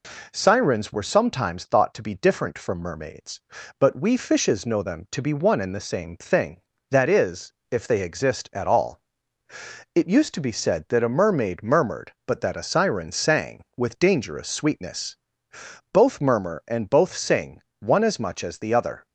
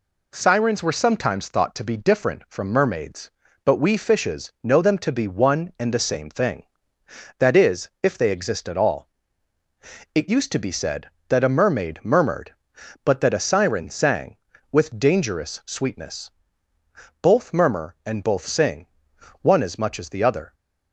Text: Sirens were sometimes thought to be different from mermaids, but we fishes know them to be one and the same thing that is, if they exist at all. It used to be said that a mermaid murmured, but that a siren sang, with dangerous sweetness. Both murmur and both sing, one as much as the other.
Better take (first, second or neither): neither